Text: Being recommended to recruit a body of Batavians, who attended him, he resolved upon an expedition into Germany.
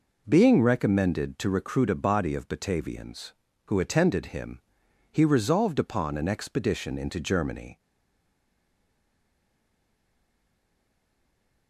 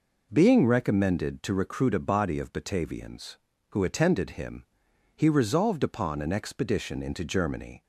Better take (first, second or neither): second